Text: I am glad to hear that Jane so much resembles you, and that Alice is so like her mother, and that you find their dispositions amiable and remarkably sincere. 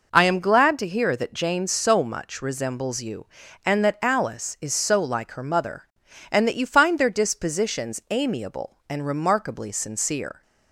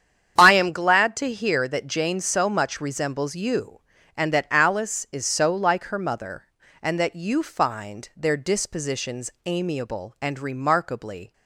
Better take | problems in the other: first | starts louder than the rest; strong; until 1.3 s; 8.5 dB // pauses between "dispositions" and "amiable"; slight; at 9.3 s; 0.16 s long // stops before "sincere"; at 11.3 s

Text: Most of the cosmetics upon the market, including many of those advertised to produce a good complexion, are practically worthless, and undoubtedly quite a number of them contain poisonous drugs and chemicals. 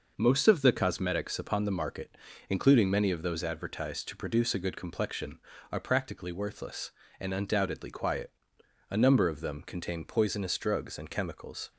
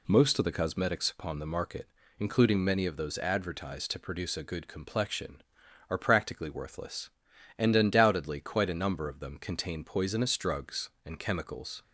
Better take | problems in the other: second | says "quiet" for "quite"; at 7.8 s

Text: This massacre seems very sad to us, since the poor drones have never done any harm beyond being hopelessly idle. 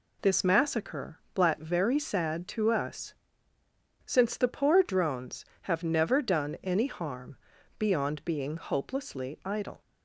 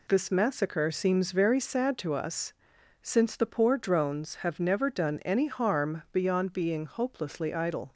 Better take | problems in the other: second | says "blat" for "seems"; at 1.3 s // pauses between "harm" and "beyond"; at 7.3 s; 0.40 s long

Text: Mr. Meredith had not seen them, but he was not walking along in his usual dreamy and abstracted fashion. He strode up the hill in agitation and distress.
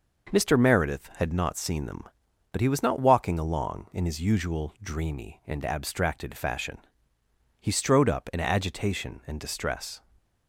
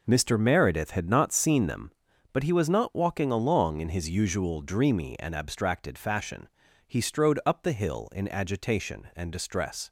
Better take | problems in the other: second | skips "the hill"; at 8.3 s // stays silent after the last word; slight; from 9.9 s on; 0.5 s long

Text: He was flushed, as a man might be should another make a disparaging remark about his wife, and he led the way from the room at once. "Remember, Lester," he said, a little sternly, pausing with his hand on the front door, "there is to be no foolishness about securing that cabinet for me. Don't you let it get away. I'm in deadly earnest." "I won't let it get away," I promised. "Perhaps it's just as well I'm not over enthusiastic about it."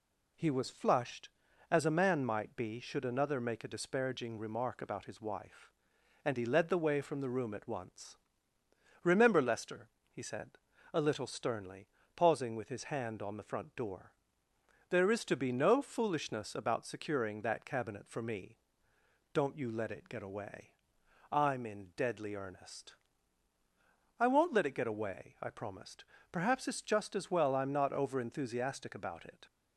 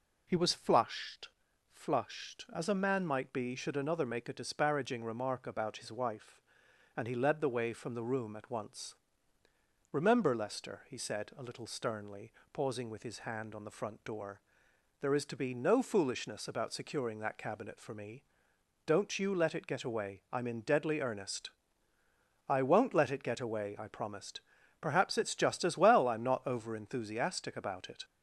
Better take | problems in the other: first | says "flushed" twice; at 1.7 s

